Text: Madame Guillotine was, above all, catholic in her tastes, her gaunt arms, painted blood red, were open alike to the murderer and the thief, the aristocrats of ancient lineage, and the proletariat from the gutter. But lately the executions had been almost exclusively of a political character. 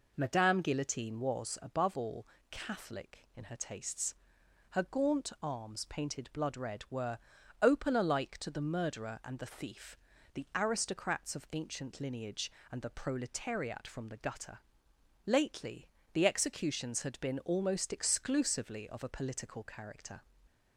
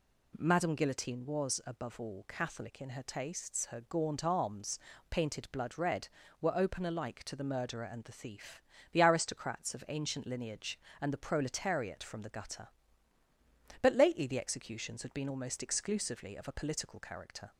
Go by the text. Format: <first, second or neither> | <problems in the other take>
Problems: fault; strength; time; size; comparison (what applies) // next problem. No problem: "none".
second | pauses between "were" and "open"; at 7.1 s; 0.44 s long // skips "But"; at 14.9 s // pauses between "lately" and "the"; slight; at 15.8 s; 0.26 s long